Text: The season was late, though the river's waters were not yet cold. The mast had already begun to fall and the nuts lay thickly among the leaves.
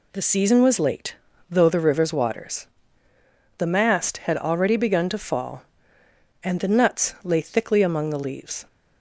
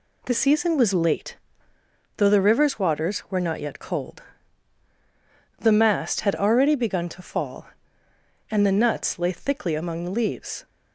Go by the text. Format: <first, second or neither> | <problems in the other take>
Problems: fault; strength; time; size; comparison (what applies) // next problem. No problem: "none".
second | skips "were not yet cold"; at 3.1 s